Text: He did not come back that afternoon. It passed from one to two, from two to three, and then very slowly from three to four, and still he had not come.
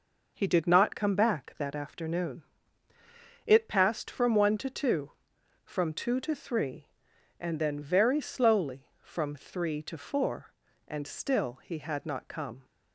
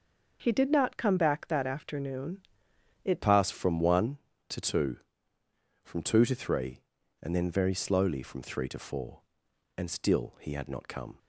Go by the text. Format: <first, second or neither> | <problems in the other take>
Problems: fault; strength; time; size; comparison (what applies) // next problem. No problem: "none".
first | starts louder than the rest; until 1.4 s; 6 dB // changes voice at "passed"; from 3.2 s on; 7.9 s long